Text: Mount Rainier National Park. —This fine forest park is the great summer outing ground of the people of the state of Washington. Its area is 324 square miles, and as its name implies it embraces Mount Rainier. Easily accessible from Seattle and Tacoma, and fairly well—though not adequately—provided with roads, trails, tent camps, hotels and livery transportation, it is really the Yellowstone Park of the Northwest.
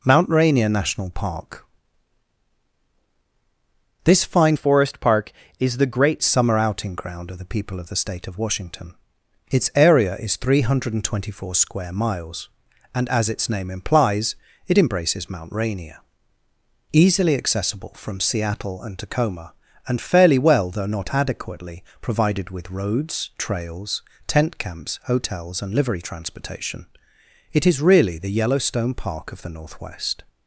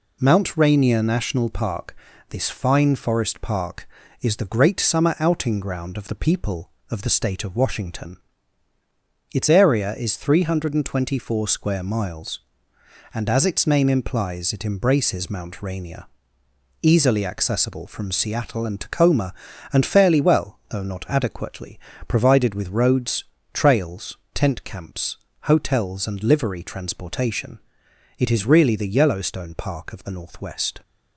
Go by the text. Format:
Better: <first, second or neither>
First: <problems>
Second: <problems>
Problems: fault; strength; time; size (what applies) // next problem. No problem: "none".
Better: second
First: changes voice from "forest" to "great"; from 4.5 to 6.2 s; 1.7 s long // pauses between "implies" and "it"; slight; at 14.3 s; 0.32 s long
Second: none